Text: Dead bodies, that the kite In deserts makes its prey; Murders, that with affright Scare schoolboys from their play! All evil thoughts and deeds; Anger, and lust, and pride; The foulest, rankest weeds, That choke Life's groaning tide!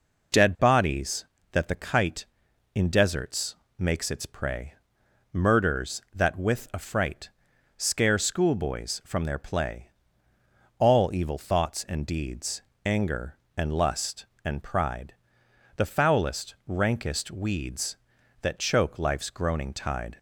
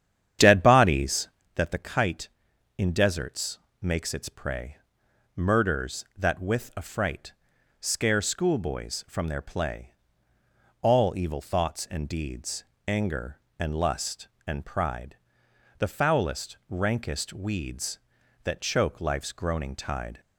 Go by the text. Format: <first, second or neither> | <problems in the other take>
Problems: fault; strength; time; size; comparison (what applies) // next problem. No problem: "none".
first | starts louder than the rest; strong; until 1.5 s; 9.5 dB // pauses between "deserts" and "makes"; slight; at 3.5 s; 0.24 s long; slight in the first // pauses between "affright" and "Scare"; noticeable; at 7.3 s; 0.48 s long; noticeable in the first